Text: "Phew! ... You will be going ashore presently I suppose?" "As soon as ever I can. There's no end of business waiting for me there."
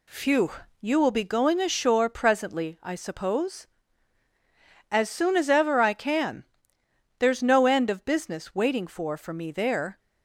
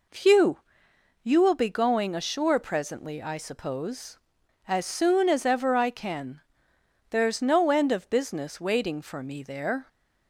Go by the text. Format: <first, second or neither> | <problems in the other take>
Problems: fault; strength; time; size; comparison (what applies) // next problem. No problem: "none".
second | says "for" twice; at 9.1 s